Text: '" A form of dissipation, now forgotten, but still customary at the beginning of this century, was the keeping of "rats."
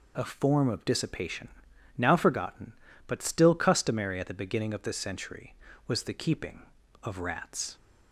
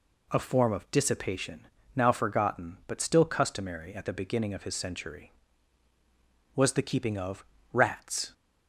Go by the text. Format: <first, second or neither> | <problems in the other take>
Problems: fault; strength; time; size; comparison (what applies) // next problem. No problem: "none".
first | says "his" for "this"; at 4.6 s // pauses between "of" and "rats"; slight; at 7.4 s; 0.26 s long